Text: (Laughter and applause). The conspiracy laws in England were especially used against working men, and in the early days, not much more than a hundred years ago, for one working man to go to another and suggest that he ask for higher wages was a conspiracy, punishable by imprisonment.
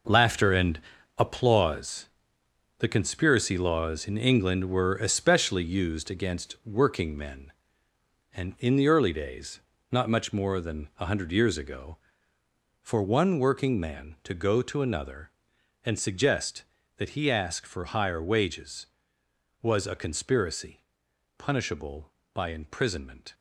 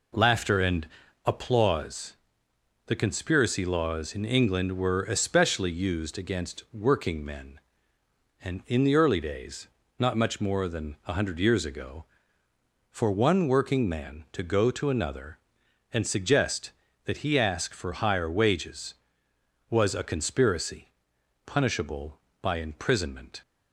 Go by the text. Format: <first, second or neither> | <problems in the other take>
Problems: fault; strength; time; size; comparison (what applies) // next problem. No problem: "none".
second | gets quieter; strong; throughout; 9.5 dB // pauses between "and" and "applause"; at 0.7 s; 0.40 s long; also in the second